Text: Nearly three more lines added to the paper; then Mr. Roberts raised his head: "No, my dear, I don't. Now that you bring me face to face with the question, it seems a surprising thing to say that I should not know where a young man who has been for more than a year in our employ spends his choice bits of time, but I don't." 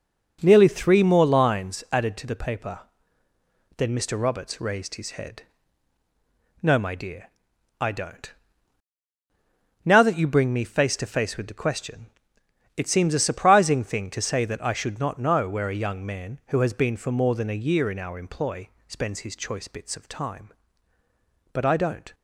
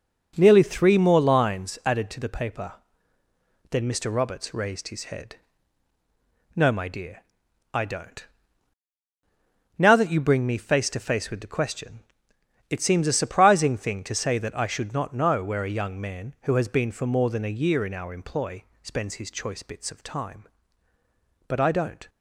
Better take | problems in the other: neither | starts louder than the rest; noticeable; the same in both // pauses between "employ" and "spends"; slight; the same in both

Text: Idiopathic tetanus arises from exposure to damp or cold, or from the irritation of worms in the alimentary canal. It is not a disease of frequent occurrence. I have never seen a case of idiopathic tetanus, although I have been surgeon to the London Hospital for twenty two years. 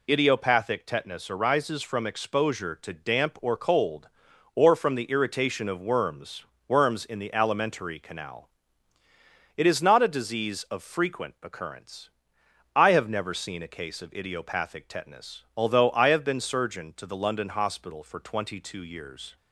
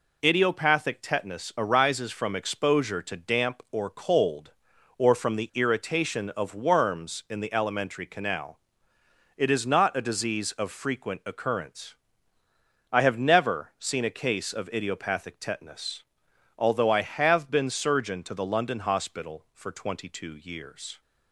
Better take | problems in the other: second | says "worms" twice; at 6.6 s

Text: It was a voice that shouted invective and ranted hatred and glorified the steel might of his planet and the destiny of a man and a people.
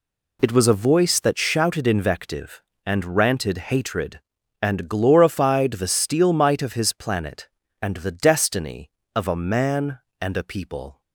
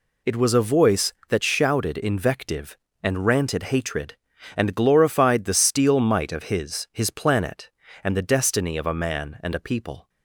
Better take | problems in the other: first | says "his" twice; at 6.9 s

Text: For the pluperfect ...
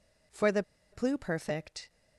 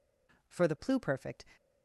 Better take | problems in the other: second | pauses between "the" and "pluperfect"; slight; at 0.6 s; 0.28 s long

